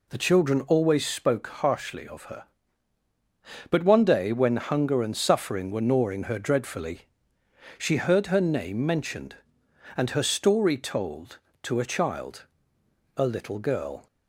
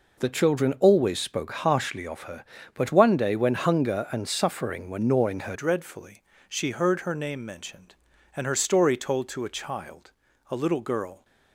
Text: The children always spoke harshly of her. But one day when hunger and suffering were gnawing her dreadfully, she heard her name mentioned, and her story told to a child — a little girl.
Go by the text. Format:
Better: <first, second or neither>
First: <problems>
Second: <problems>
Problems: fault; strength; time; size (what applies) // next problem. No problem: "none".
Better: first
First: none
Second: changes voice at "dreadfully"; from 5.5 s on; 5.7 s long